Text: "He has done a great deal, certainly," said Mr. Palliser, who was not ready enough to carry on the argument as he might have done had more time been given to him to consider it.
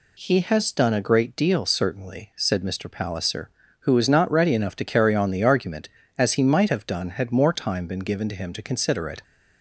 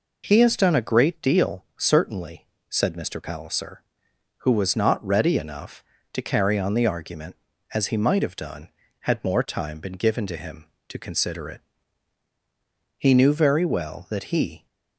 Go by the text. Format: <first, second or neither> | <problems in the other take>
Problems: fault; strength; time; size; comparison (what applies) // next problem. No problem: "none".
first | goes on to say "He knew very well that he"; strong; from 12.9 s on; 1.6 s long